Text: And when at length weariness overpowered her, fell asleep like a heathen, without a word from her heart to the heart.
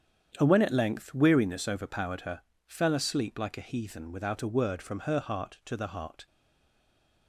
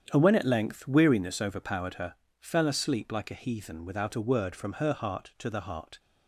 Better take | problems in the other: second | starts louder than the rest; strong; until 1.4 s; 8.5 dB; strong in the second // stays silent after the last word; from 6.2 s on; 1.0 s long

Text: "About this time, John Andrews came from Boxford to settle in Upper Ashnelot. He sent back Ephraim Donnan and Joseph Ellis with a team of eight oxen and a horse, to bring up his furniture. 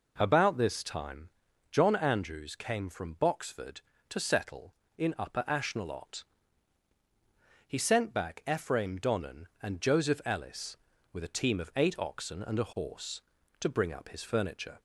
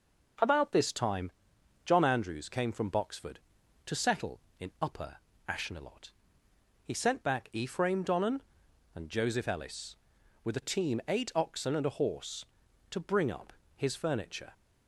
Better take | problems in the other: first | pauses between "Upper" and "Ashnelot"; slight; at 5.1 s; 0.30 s long // skips "of"; at 11.0 s // pauses between "up" and "his"; slight; at 13.5 s; 0.24 s long

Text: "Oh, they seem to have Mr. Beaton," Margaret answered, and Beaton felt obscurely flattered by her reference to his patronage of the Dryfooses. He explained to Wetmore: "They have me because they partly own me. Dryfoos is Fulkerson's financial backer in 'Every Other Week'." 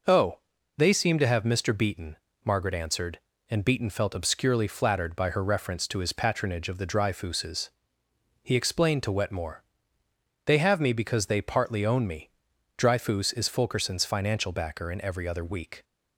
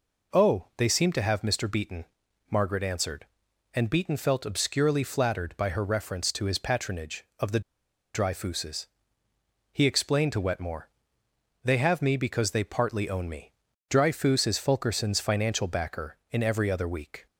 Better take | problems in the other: first | pauses between "the" and "Dryfooses"; noticeable; at 7.6 s; 0.54 s long

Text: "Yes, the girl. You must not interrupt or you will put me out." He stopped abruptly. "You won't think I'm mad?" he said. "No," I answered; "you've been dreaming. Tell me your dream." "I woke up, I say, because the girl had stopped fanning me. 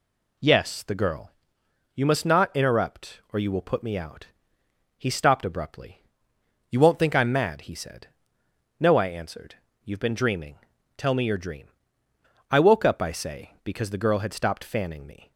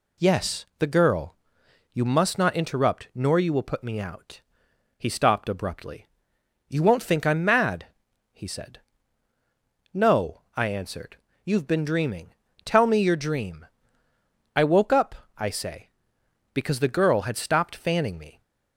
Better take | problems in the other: first | says "nor" for "or"; at 3.1 s

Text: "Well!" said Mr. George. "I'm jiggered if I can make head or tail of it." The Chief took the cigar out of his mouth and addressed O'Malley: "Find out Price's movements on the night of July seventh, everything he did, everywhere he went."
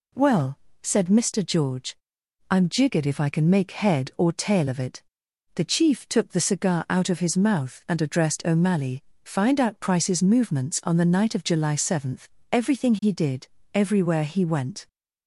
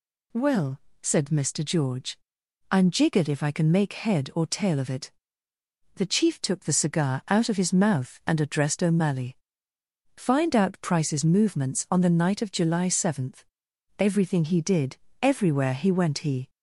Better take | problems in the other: first | goes on to say "He"; slight; from 16.1 s on; 0.30 s long

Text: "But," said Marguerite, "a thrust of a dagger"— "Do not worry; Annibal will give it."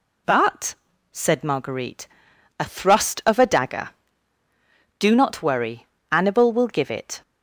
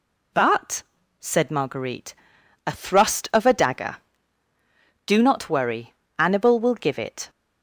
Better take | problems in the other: neither | none

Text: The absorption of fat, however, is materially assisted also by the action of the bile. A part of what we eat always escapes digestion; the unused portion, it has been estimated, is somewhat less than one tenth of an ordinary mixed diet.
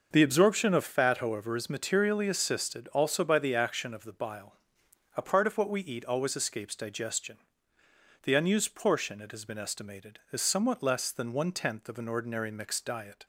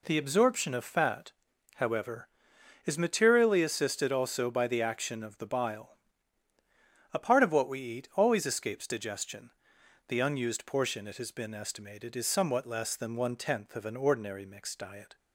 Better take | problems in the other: neither | none

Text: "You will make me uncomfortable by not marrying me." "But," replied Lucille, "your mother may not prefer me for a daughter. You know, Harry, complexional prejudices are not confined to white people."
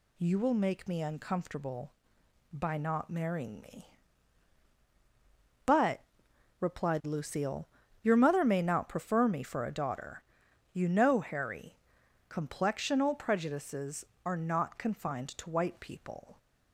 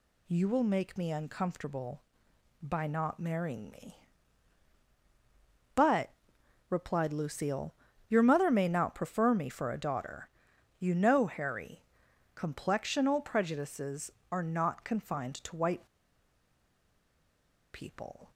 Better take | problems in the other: first | pauses between "white" and "people"; strong; at 15.8 s; 1.8 s long

